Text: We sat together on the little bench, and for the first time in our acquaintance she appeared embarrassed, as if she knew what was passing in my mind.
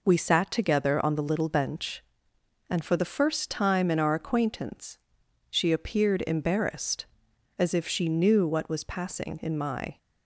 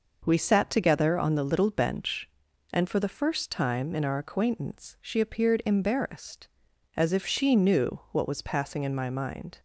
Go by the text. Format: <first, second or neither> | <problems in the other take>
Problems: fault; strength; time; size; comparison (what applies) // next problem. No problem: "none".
second | pauses between "acquaintance" and "she"; noticeable; at 4.9 s; 0.50 s long // stops before "mind"; at 9.9 s